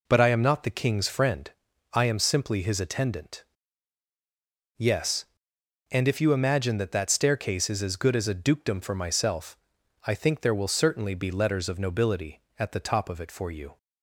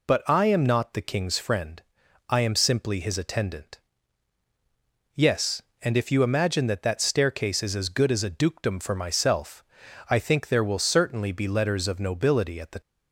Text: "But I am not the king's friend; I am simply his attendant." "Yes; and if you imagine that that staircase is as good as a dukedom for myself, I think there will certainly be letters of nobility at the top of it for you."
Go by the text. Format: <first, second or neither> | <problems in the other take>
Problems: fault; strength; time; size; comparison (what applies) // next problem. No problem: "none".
first | stops before "top of it for you"; at 12.8 s